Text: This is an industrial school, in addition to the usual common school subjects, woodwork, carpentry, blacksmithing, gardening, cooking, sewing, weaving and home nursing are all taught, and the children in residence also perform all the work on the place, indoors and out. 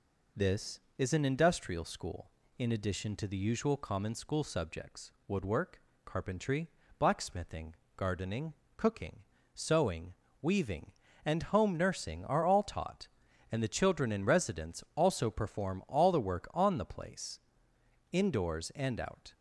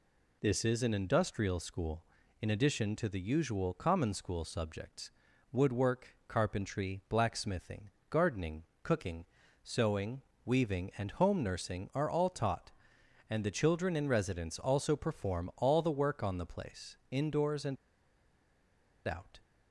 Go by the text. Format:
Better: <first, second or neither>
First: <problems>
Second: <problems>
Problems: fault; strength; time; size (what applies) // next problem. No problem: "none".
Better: first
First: none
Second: pauses between "and" and "out"; strong; at 17.7 s; 1.3 s long